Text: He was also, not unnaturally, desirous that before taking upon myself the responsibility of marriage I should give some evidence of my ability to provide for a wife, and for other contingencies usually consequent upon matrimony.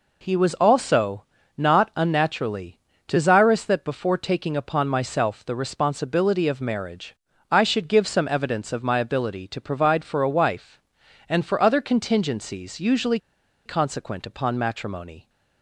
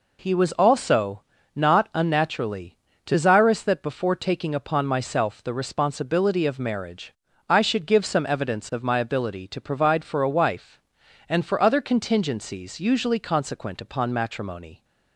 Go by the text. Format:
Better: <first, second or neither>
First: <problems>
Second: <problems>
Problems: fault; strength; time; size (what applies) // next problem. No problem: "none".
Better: second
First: pauses between "marriage" and "I"; slight; at 7.1 s; 0.34 s long // pauses between "usually" and "consequent"; noticeable; at 13.1 s; 0.47 s long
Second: pauses between "marriage" and "I"; slight; at 7.1 s; 0.34 s long